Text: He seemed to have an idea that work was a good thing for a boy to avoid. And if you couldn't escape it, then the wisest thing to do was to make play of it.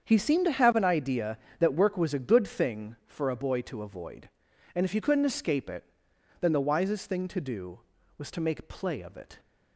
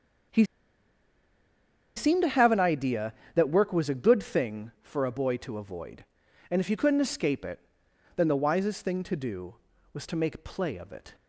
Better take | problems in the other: first | starts louder than the rest; strong; until 2.8 s; 7.5 dB; strong in the first // pauses between "He" and "seemed"; strong; at 0.4 s; 1.5 s long

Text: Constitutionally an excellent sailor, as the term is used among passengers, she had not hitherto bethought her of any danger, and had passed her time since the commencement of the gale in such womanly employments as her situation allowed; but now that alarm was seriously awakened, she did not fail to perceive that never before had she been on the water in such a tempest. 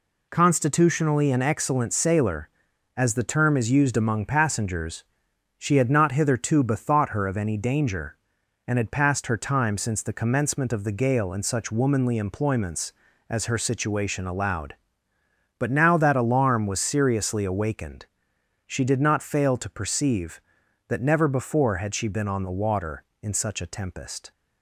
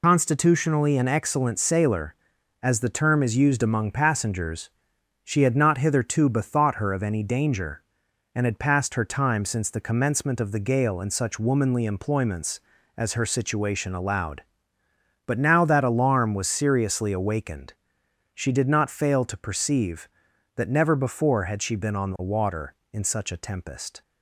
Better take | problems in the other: first | loses the start of "Constitutionally"; at 0.0 s; 75 ms

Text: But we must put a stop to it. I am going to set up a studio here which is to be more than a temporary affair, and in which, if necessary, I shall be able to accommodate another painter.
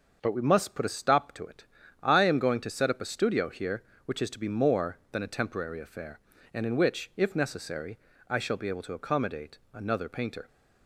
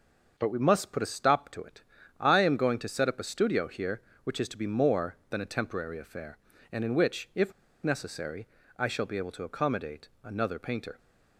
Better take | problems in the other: first | starts louder than the rest; until 1.3 s; 6.5 dB; also in the first // pauses between "if" and "necessary"; slight; at 7.5 s; 0.30 s long // pauses between "accommodate" and "another"; slight; at 10.0 s; 0.16 s long; slight in the first

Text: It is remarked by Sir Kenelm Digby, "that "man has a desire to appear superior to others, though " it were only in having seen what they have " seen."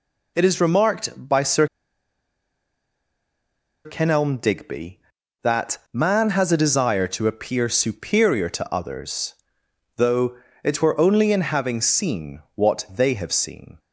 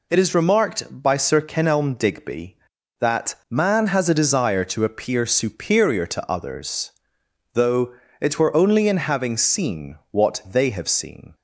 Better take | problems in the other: second | pauses between "Sir" and "Kenelm"; strong; at 1.6 s; 2.1 s long

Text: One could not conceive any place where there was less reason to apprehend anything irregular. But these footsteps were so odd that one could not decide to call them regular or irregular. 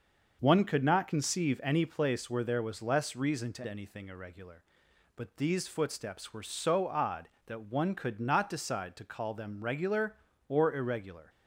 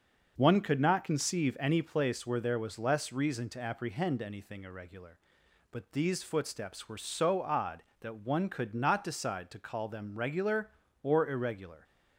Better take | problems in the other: second | starts louder than the rest; until 1.4 s; 6 dB; noticeable in the second // skips "apprehend"; at 3.6 s

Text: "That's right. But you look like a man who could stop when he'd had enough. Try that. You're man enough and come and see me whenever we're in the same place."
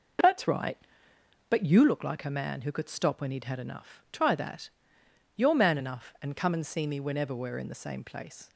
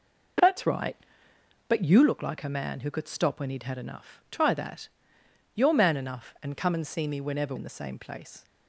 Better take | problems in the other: first | skips "we're"; at 7.5 s

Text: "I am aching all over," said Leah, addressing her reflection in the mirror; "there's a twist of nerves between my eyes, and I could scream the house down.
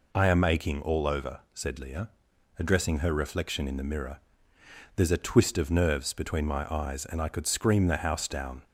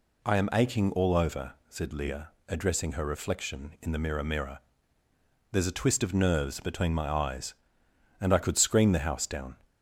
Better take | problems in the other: first | says "mirror" twice; at 4.2 s

